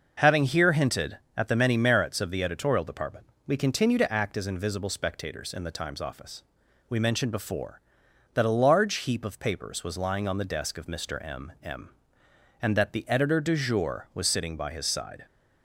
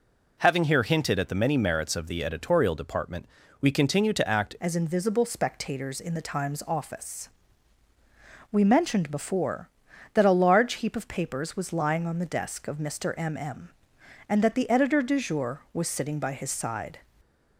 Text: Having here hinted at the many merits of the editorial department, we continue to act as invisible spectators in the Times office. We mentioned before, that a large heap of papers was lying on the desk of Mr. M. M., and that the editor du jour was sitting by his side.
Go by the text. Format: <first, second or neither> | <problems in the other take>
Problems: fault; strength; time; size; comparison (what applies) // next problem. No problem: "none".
first | changes voice at "as"; from 4.5 s on; 12.4 s long